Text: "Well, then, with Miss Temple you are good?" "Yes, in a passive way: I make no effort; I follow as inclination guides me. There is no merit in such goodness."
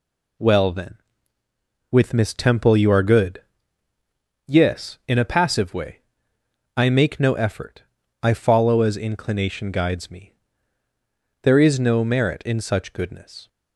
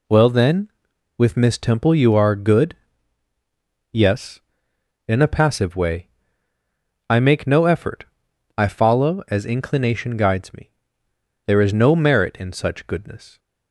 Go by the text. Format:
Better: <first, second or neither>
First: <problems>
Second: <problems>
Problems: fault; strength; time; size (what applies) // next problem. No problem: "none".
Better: neither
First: none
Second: none